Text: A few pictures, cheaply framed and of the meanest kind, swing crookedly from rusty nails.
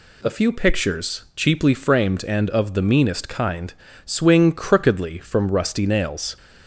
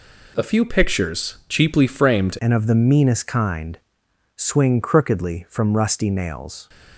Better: first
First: none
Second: changes voice at "and"; from 2.3 s on; 4.3 s long

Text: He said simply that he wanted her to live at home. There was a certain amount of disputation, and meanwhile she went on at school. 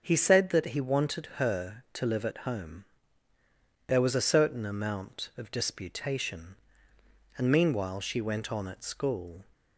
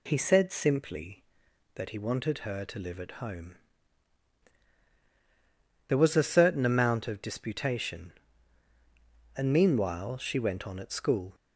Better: second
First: starts louder than the rest; until 1.0 s; 6.5 dB // skips "simply"; at 0.5 s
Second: none

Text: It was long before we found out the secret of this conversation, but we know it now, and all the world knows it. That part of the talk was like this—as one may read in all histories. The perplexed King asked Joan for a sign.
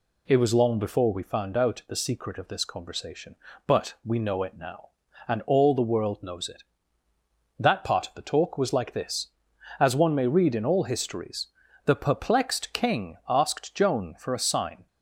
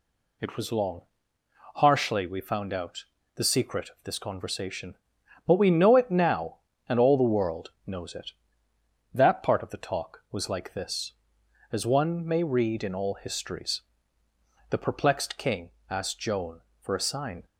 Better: first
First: none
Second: says "harshly" for "before"; at 1.7 s // pauses between "out" and "the"; slight; at 3.0 s; 0.32 s long // pauses between "King" and "asked"; slight; at 15.7 s; 0.18 s long

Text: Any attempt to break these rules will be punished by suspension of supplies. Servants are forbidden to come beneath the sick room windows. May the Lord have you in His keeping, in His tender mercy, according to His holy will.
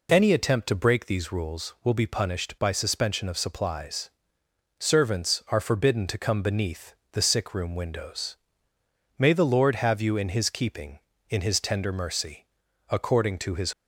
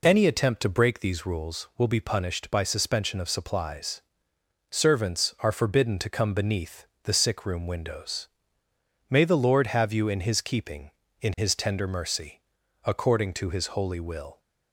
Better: second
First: pauses between "beneath" and "the"; slight; at 6.9 s; 0.20 s long // stops before "holy will"; at 13.7 s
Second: pauses between "beneath" and "the"; slight; at 6.8 s; 0.20 s long

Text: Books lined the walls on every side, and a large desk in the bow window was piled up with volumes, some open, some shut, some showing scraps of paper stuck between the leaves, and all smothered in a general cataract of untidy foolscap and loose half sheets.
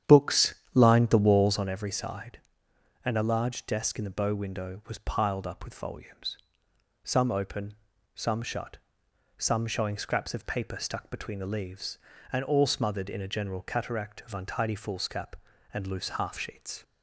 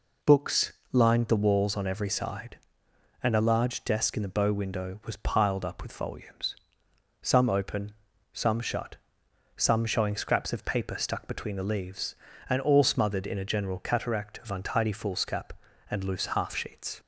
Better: second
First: starts louder than the rest; strong; until 1.7 s; 9.5 dB // pauses between "Books" and "lined"; slight; at 0.5 s; 0.20 s long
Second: pauses between "Books" and "lined"; slight; at 0.7 s; 0.20 s long

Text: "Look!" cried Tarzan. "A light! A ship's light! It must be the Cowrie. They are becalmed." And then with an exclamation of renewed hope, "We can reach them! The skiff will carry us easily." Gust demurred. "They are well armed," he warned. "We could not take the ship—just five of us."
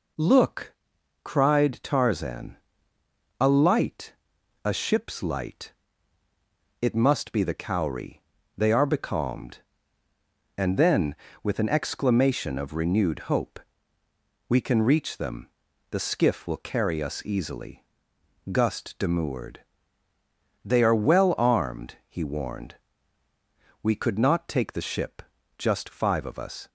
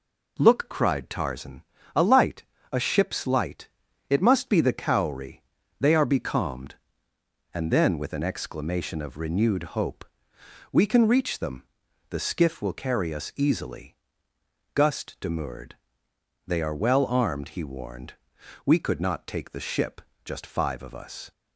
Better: neither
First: none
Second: none

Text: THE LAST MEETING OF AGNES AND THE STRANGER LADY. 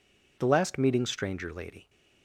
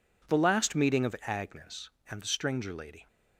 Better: second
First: skips "OF AGNES AND THE"; at 1.0 s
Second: none

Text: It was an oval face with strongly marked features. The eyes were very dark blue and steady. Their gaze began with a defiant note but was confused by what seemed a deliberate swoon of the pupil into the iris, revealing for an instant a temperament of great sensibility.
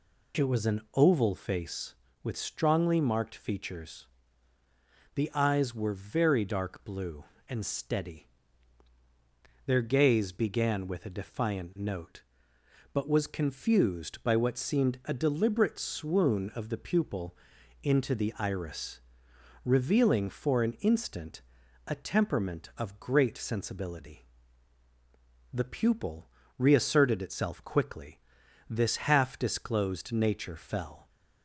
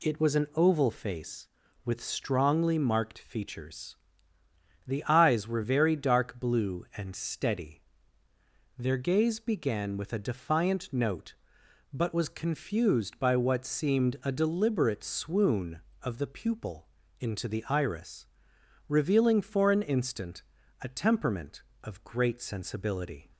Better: second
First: pauses between "pupil" and "into"; noticeable; at 17.3 s; 0.46 s long // pauses between "instant" and "a"; at 21.4 s; 0.44 s long // goes on to say "The pupil reasserted itself quickly this half disclosed nature fell"; strong; from 25.5 s on; 5.5 s long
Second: pauses between "pupil" and "into"; slight; at 16.8 s; 0.32 s long // pauses between "instant" and "a"; at 20.4 s; 0.38 s long

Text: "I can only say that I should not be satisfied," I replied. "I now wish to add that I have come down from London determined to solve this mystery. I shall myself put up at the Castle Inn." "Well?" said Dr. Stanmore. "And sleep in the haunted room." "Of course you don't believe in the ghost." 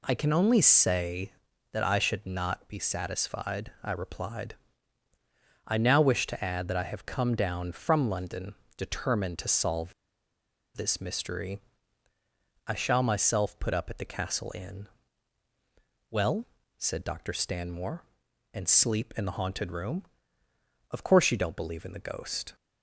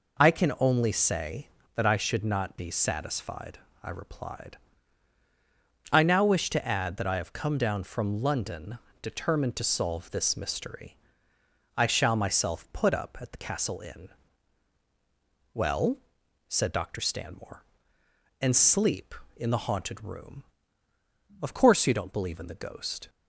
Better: second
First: pauses between "London" and "determined"; slight; at 8.5 s; 0.22 s long // pauses between "solve" and "this"; noticeable; at 9.9 s; 0.83 s long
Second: pauses between "London" and "determined"; slight; at 8.7 s; 0.22 s long

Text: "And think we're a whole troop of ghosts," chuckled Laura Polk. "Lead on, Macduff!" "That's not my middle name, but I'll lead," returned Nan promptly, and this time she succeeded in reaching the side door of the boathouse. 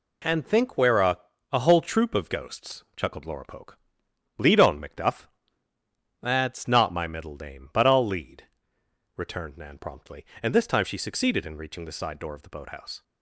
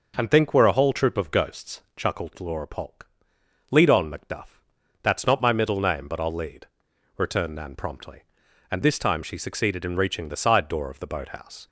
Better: second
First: says "a" twice; at 1.5 s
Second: none

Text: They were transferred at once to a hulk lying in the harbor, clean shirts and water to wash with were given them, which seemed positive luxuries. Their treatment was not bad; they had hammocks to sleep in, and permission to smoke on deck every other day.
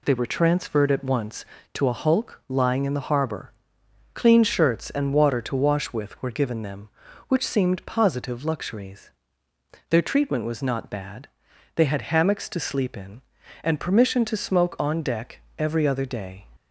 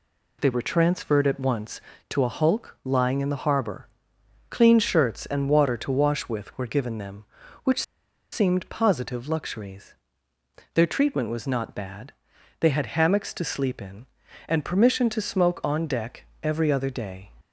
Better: first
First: pauses between "deck" and "every"; slight; at 15.3 s; 0.18 s long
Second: pauses between "which" and "seemed"; noticeable; at 7.8 s; 0.50 s long // pauses between "deck" and "every"; slight; at 16.2 s; 0.18 s long

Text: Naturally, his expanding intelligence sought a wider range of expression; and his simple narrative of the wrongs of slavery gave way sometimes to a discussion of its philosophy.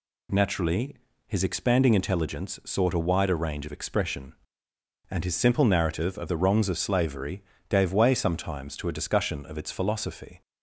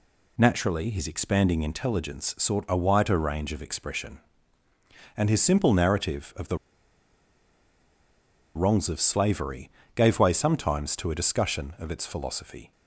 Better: first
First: pauses between "slavery" and "gave"; slight; at 7.4 s; 0.26 s long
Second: pauses between "the" and "wrongs"; strong; at 6.5 s; 1.9 s long // pauses between "slavery" and "gave"; slight; at 9.6 s; 0.24 s long

